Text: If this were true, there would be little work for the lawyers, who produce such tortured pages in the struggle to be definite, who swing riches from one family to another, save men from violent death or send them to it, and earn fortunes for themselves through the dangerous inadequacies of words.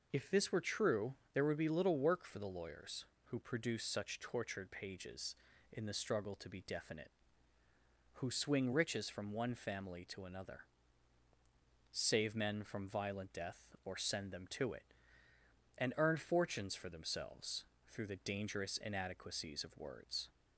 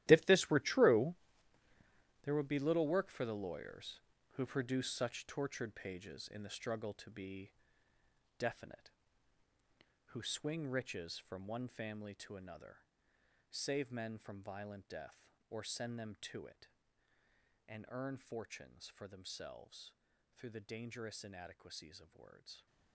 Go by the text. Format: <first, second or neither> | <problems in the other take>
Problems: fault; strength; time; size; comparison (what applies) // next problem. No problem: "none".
first | gets quieter; strong; throughout; 14 dB // pauses between "be" and "definite"; noticeable; at 7.5 s; 0.86 s long // pauses between "themselves" and "through"; at 19.9 s; 0.42 s long; slight in the first